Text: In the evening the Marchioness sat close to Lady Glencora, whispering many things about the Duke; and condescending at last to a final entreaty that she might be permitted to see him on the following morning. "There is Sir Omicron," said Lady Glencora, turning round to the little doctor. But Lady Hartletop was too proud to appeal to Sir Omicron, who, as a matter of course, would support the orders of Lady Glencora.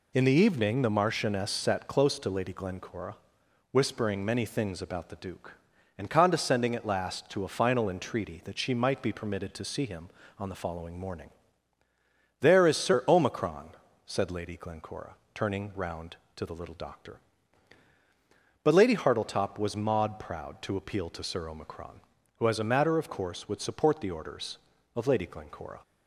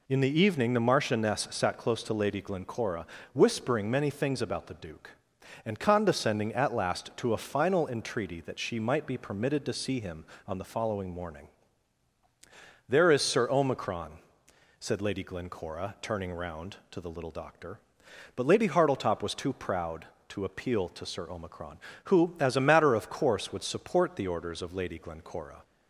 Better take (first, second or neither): second